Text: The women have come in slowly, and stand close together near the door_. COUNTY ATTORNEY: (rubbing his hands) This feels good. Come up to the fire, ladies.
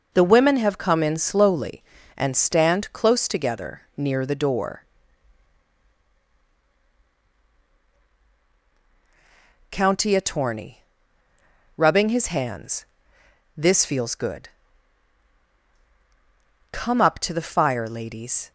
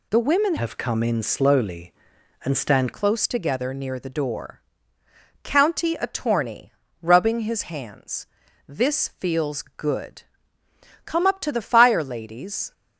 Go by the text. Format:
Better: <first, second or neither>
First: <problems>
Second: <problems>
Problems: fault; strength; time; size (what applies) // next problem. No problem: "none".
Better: first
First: none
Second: changes voice from "have" to "stand"; from 0.5 to 2.9 s; 2.4 s long